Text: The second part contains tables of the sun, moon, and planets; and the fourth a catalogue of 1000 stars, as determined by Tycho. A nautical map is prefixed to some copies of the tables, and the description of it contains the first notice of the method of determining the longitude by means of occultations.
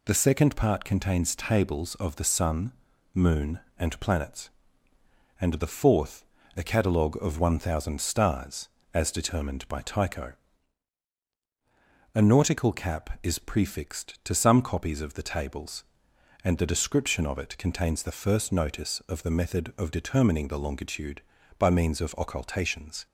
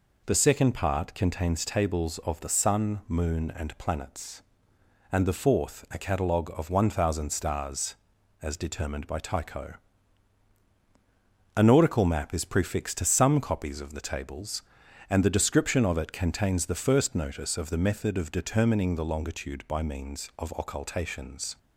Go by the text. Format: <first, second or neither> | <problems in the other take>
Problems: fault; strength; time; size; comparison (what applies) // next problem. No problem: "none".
second | pauses between "fourth" and "a"; slight; at 6.2 s; 0.32 s long // says "cap" for "map"; at 12.7 s